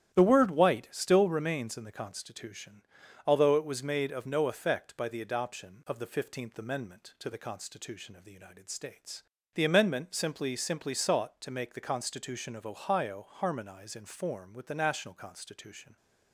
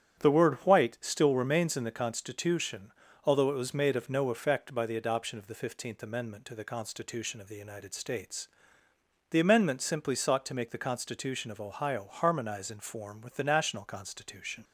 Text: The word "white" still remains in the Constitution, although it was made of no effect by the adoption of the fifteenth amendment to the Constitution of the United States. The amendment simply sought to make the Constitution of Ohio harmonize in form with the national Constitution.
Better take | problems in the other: second | starts louder than the rest; strong; until 1.1 s; 11 dB; strong in the second // says "simply" twice; at 10.5 s

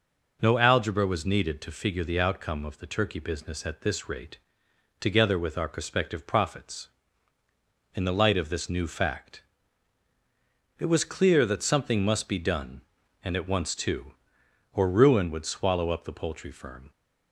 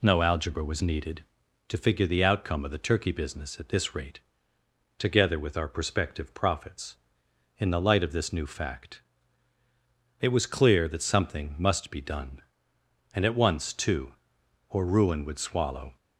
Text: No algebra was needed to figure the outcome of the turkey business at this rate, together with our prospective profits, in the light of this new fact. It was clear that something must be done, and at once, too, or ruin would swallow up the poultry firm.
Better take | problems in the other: first | stops before "up the poultry firm"; at 15.9 s

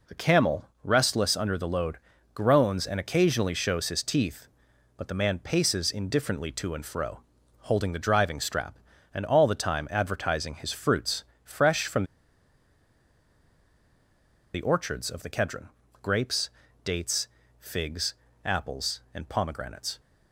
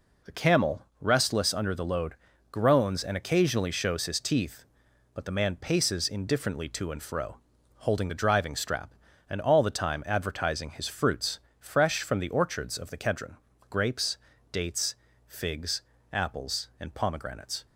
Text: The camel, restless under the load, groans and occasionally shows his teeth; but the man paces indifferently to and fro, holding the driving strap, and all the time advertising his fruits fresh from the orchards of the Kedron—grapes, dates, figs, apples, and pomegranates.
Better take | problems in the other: second | pauses between "fruits" and "fresh"; slight; at 11.2 s; 0.20 s long; slight in the second // pauses between "from" and "the"; strong; at 12.0 s; 2.5 s long

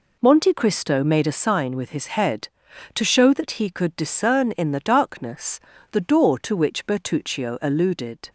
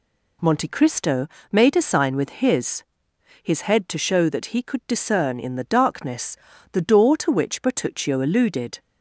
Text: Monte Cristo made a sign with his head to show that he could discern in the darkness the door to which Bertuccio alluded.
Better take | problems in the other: first | pauses between "Cristo" and "made"; slight; at 1.2 s; 0.24 s long // says "his" twice; at 3.4 s // pauses between "darkness" and "the"; slight; at 6.3 s; 0.36 s long; slight in the first

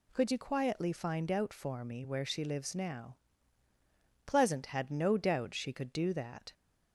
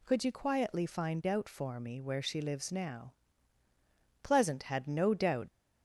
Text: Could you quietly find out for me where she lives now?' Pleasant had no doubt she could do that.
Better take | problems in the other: first | stops before "she could do that"; at 5.4 s

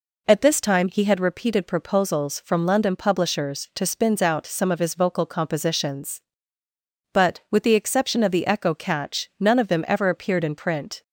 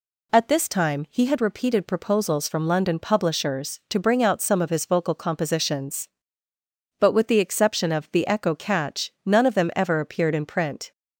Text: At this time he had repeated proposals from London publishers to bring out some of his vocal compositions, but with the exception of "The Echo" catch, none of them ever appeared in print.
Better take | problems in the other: second | says "spins" for "bring"; at 3.8 s

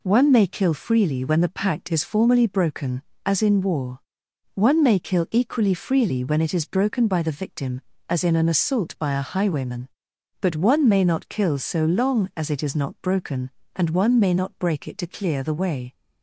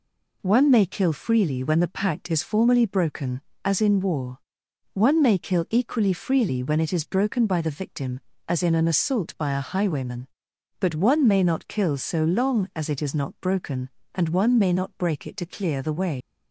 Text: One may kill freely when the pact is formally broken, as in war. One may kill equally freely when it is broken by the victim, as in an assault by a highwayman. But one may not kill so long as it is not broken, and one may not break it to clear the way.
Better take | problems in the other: first | leaves "way" unfinished; at 16.2 s; 110 ms

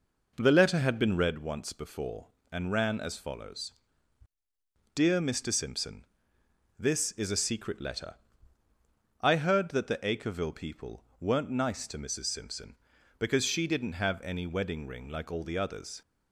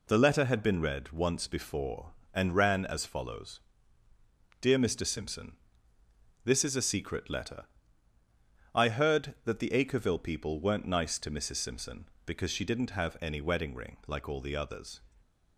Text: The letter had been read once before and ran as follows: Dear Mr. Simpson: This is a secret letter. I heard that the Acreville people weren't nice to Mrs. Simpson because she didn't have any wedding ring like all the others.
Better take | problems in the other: second | starts louder than the rest; noticeable; until 1.3 s; 5 dB // pauses between "people" and "weren't"; slight; at 11.0 s; 0.16 s long

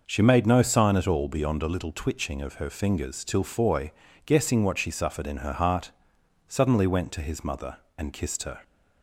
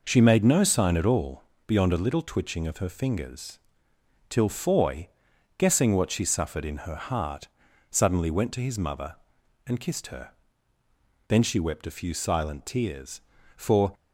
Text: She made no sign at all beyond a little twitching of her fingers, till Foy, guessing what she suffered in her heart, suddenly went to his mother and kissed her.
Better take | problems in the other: first | pauses between "all" and "beyond"; slight; at 1.4 s; 0.24 s long // goes on to say "Then she wept a few silent tears for"; strong; from 11.2 s on; 2.6 s long

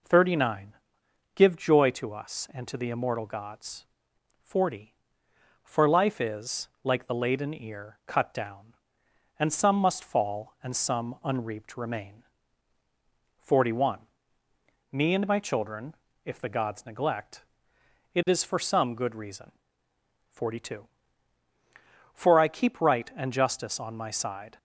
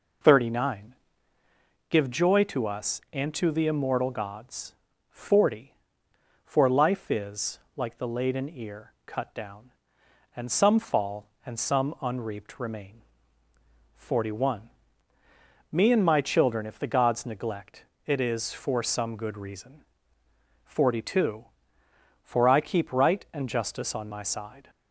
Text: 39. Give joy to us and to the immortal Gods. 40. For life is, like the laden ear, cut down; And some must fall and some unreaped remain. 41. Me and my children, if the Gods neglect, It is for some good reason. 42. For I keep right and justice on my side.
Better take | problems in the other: first | skips "must"; at 10.7 s

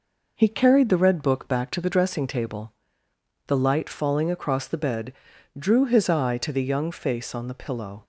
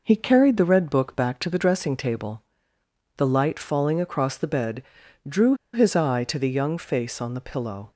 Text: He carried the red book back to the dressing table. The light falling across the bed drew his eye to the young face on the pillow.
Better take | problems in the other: first | pauses between "bed" and "drew"; at 4.8 s; 0.44 s long; also in the first // pauses between "drew" and "his"; slight; at 5.5 s; 0.19 s long

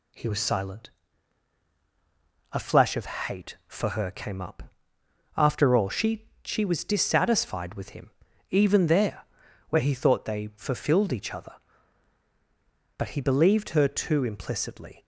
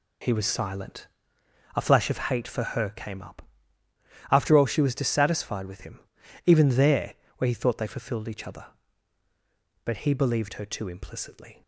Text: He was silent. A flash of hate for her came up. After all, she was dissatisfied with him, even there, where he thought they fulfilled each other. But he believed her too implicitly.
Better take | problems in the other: second | says "she" twice; at 6.4 s

